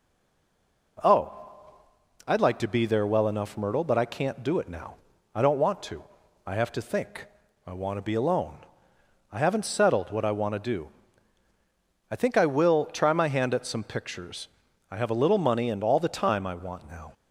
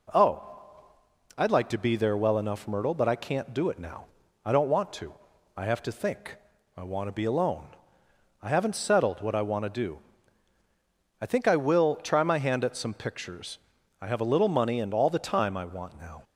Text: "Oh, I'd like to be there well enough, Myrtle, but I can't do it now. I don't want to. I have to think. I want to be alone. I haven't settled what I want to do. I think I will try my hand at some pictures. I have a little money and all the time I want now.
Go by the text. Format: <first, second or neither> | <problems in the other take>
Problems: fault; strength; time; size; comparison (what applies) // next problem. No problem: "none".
second | stays silent before the first word; slight; until 0.9 s; 0.9 s long